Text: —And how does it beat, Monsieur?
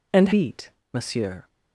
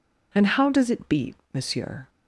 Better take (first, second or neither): second